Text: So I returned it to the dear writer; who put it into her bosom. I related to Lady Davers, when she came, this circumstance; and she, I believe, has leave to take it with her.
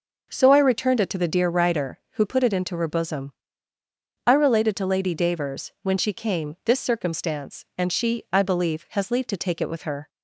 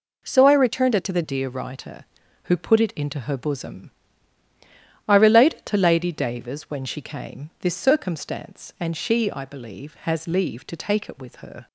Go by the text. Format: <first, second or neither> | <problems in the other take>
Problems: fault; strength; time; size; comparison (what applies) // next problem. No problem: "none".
first | changes voice at "dear"; from 1.2 s on; 10.4 s long